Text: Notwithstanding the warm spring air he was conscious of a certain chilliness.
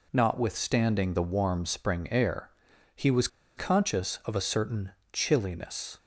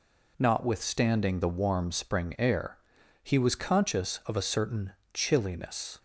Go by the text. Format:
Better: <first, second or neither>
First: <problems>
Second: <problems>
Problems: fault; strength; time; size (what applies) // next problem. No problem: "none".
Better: second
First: pauses between "air" and "he"; noticeable; at 2.4 s; 0.46 s long // pauses between "was" and "conscious"; slight; at 3.2 s; 0.29 s long // pauses between "certain" and "chilliness"; slight; at 4.9 s; 0.20 s long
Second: pauses between "air" and "he"; noticeable; at 2.7 s; 0.46 s long // pauses between "certain" and "chilliness"; slight; at 4.9 s; 0.20 s long